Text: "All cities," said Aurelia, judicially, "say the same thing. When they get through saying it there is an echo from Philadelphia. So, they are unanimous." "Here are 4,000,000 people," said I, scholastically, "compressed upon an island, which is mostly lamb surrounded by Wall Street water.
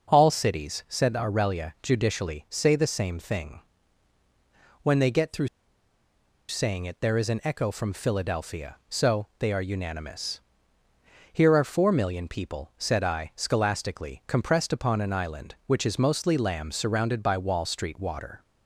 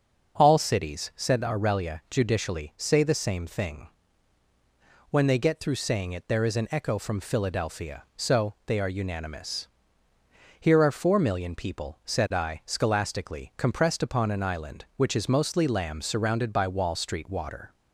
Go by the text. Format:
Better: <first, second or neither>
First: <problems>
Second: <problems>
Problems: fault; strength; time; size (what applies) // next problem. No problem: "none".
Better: second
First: starts louder than the rest; until 1.1 s; 6 dB // pauses between "through" and "saying"; at 5.4 s; 1.0 s long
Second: starts louder than the rest; until 1.4 s; 6 dB